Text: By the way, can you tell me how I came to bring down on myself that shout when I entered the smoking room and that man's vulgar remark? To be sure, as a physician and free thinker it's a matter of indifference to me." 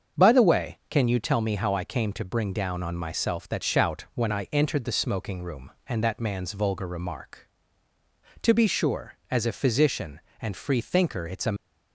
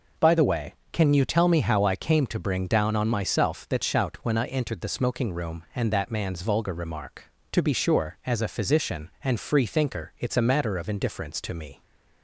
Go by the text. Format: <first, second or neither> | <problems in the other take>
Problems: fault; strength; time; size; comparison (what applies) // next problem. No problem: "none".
second | starts louder than the rest; until 1.2 s; 7 dB // stops before "matter of indifference to me"; at 11.5 s